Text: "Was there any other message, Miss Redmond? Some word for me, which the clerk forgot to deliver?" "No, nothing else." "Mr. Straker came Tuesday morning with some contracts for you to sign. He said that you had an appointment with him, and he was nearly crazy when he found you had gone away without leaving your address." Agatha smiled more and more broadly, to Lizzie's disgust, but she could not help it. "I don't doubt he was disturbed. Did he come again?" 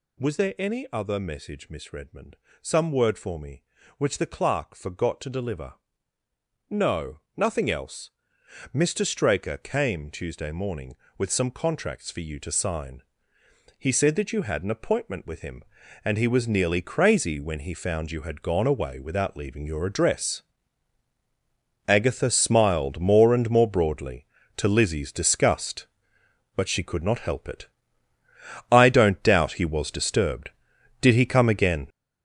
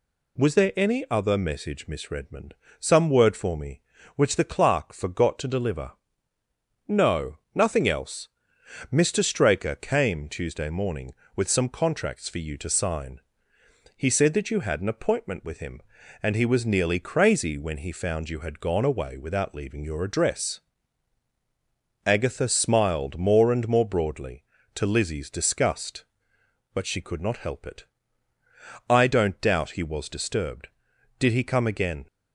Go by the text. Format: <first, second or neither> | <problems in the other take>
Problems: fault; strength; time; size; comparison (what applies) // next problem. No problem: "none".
second | gets louder; strong; throughout; 9 dB